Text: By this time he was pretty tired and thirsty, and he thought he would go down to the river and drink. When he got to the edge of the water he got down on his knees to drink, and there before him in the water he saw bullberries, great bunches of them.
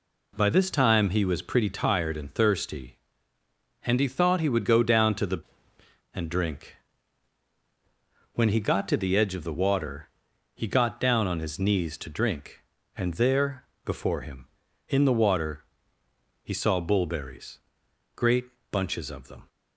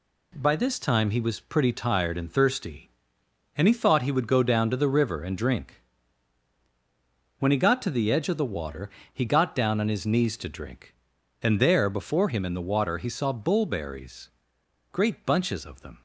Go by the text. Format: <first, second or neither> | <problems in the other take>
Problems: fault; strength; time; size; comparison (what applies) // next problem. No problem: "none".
second | skips "river"; at 5.7 s // pauses between "water" and "he"; noticeable; at 10.0 s; 0.46 s long; slight in the second // pauses between "there" and "before"; slight; at 13.6 s; 0.20 s long // pauses between "water" and "he"; noticeable; at 15.6 s; 0.78 s long // pauses between "great" and "bunches"; slight; at 18.4 s; 0.24 s long